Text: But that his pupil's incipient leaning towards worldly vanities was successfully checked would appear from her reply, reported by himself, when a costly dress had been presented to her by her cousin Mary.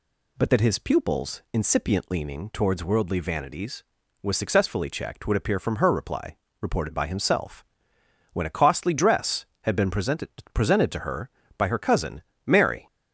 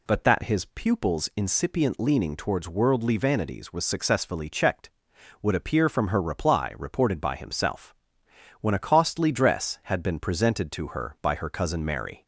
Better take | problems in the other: second | says "presented" twice; at 10.5 s // pauses between "cousin" and "Mary"; slight; at 12.2 s; 0.22 s long

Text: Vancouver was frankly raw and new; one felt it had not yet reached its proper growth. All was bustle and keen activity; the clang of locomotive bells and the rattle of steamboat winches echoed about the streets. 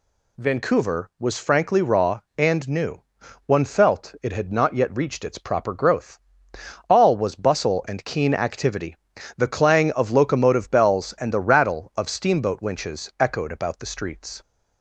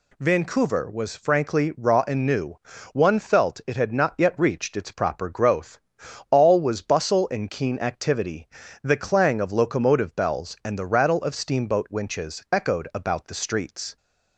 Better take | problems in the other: neither | none

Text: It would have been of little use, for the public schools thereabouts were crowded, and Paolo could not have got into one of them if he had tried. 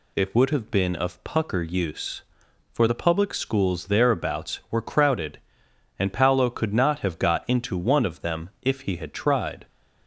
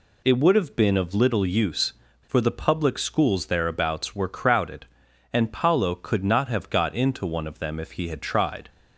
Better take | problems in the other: second | says "pucker" for "little"; at 1.2 s

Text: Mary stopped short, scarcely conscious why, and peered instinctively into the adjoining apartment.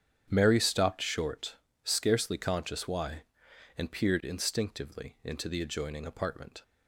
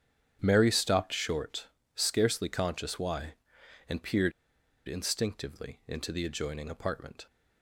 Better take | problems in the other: first | starts louder than the rest; strong; until 1.4 s; 9 dB; strong in the first // pauses between "peered" and "instinctively"; noticeable; at 4.3 s; 0.56 s long

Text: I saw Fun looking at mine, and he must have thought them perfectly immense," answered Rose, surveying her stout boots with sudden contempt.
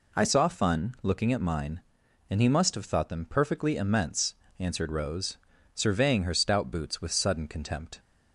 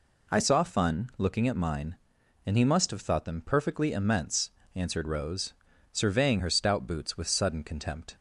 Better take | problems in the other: neither | none

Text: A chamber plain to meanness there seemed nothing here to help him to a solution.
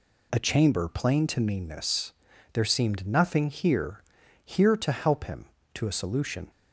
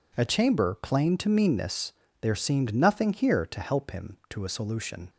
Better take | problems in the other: second | pauses between "meanness" and "there"; at 2.1 s; 0.40 s long; slight in the second // says "here" twice; at 4.4 s

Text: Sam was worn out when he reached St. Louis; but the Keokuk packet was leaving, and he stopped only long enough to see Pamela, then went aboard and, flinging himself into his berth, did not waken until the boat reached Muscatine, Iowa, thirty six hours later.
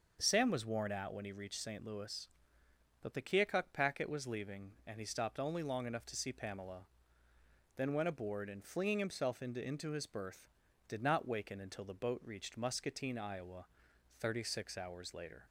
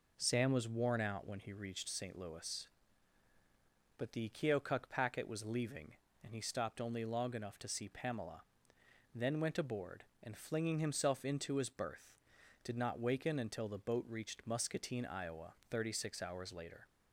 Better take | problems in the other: second | starts louder than the rest; noticeable; until 1.2 s; 6 dB // says "into" twice; at 9.6 s

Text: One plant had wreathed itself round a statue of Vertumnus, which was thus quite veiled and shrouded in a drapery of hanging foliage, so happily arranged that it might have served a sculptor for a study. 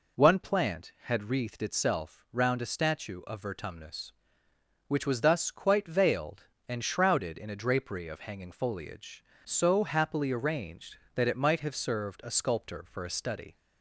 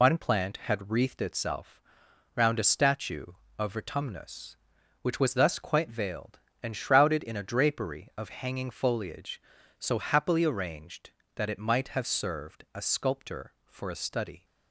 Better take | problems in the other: first | loses the start of "One"; at 0.0 s; 65 ms // pauses between "itself" and "round"; noticeable; at 1.7 s; 0.54 s long

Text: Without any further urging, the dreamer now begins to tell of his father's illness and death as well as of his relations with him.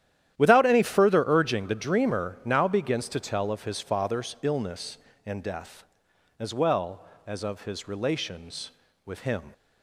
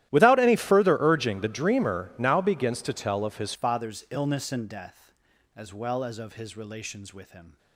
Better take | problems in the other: first | starts louder than the rest; strong; until 1.1 s; 14 dB; strong in the first // changes voice at "father's"; from 3.5 s on; 4.0 s long

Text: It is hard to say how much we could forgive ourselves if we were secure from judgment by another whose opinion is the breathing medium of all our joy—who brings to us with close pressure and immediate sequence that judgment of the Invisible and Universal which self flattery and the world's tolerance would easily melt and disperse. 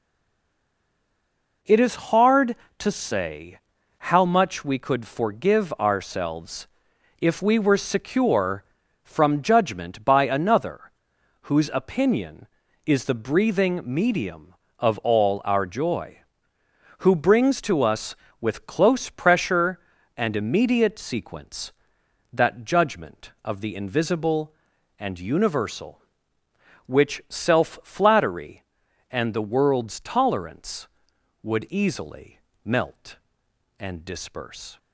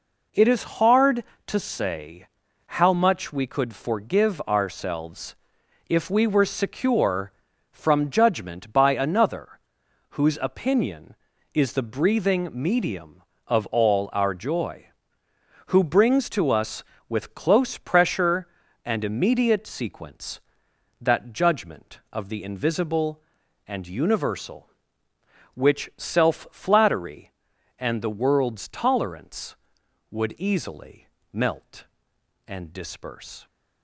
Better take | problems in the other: second | stays silent before the first word; noticeable; until 1.6 s; 1.6 s long // pauses between "say" and "how"; noticeable; at 3.5 s; 0.50 s long; noticeable in the second // pauses between "ourselves" and "if"; noticeable; at 6.6 s; 0.54 s long; noticeable in the second // pauses between "another" and "whose"; noticeable; at 10.8 s; 0.52 s long; noticeable in the second // pauses between "easily" and "melt"; slight; at 32.3 s; 0.26 s long; slight in the second

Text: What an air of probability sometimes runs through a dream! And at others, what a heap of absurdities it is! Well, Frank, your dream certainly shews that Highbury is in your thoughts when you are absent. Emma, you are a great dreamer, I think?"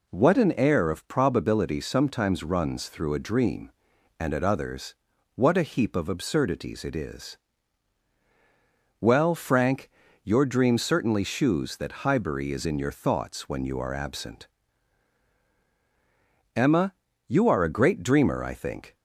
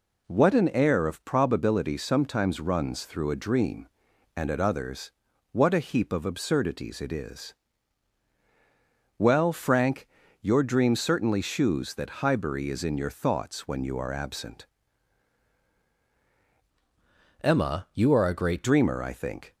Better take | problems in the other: first | changes voice from "Emma" to "great"; from 17.4 to 18.6 s; 1.2 s long

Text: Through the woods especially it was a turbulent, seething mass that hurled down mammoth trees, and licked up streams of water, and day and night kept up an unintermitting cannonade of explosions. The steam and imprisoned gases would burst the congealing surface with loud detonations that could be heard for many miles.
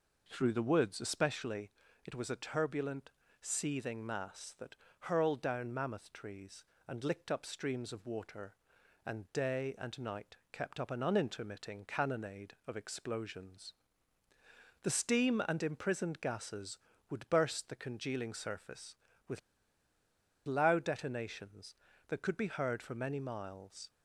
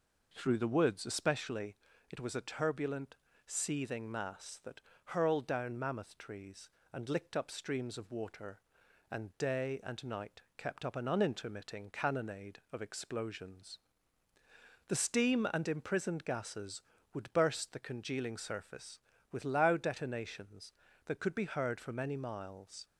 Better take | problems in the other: second | pauses between "especially" and "it"; slight; at 1.7 s; 0.34 s long; slight in the second // pauses between "that" and "hurled"; slight; at 4.7 s; 0.26 s long; slight in the second // pauses between "night" and "kept"; slight; at 10.3 s; 0.16 s long; slight in the second // pauses between "with" and "loud"; at 19.3 s; 1.0 s long

